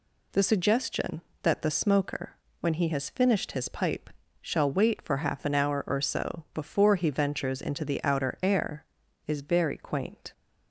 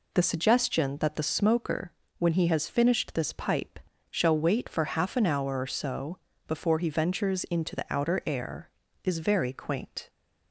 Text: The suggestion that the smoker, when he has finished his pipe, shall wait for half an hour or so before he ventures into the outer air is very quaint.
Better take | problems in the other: first | says "this" for "his"; at 3.1 s // pauses between "so" and "before"; slight; at 6.1 s; 0.30 s long

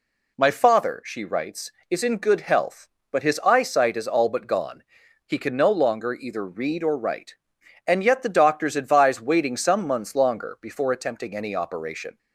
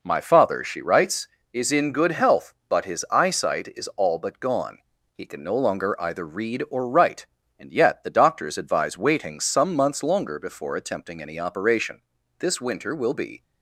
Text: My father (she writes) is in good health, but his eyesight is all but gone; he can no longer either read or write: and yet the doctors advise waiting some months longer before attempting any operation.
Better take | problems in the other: first | goes on to say "This winter will be"; noticeable; from 12.3 s on; 1.0 s long

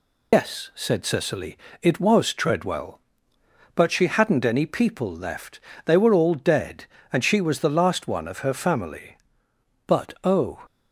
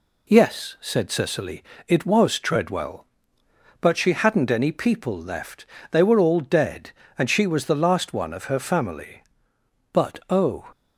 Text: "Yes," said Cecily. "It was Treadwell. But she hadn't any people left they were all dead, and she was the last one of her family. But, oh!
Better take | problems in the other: second | loses the start of "Yes"; at 0.3 s; 95 ms // pauses between "left" and "they"; slight; at 5.5 s; 0.26 s long; slight in the second

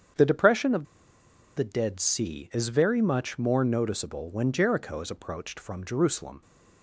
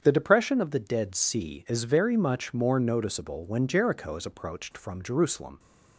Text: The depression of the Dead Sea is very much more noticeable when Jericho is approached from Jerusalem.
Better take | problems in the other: second | starts louder than the rest; strong; until 1.8 s; 8 dB; strong in the second // pauses between "of" and "the"; noticeable; at 0.8 s; 0.72 s long

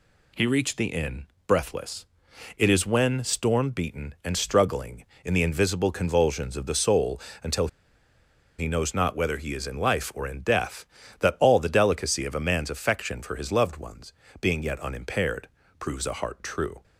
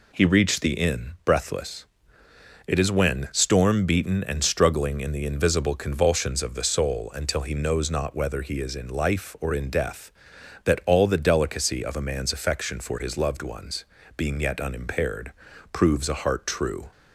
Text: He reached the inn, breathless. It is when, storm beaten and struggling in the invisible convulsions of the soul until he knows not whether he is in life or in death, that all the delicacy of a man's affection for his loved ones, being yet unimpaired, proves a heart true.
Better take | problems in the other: second | pauses between "soul" and "until"; slight; at 7.1 s; 0.24 s long // pauses between "until" and "he"; noticeable; at 7.6 s; 0.90 s long

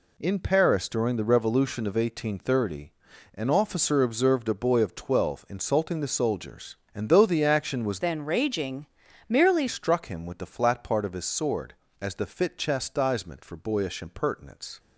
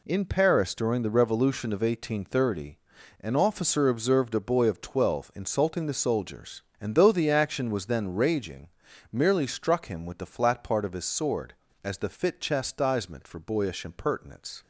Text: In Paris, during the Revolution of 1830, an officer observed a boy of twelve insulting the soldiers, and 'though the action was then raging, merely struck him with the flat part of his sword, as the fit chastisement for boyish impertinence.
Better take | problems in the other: second | changes voice from "then" to "merely"; from 8.0 to 9.6 s; 1.6 s long

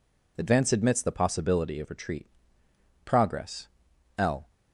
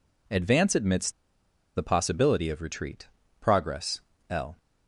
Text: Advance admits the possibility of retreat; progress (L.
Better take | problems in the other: first | pauses between "admits" and "the"; noticeable; at 1.1 s; 0.63 s long

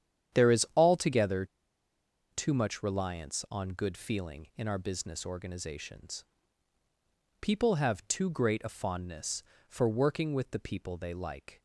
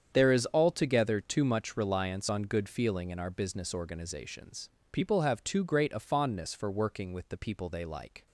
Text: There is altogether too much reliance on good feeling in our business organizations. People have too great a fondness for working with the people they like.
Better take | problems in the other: second | starts louder than the rest; strong; until 1.4 s; 9.5 dB; strong in the second // pauses between "altogether" and "too"; noticeable; at 1.4 s; 0.85 s long

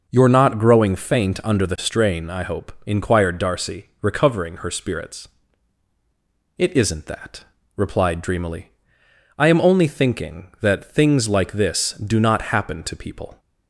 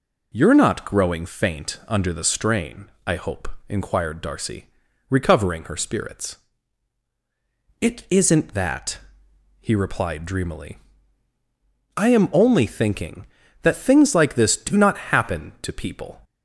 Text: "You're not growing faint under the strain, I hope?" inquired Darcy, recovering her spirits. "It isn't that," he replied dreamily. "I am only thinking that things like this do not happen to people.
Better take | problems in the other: second | skips "he"; at 7.5 s

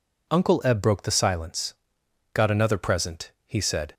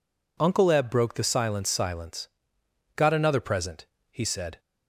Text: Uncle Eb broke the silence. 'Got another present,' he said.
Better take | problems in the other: first | says "silence" twice; at 1.6 s

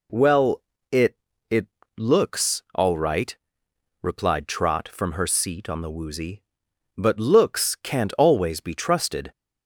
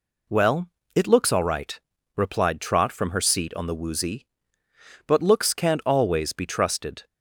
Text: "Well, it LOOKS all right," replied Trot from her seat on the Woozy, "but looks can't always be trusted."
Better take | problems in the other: second | says "it" twice; at 1.4 s

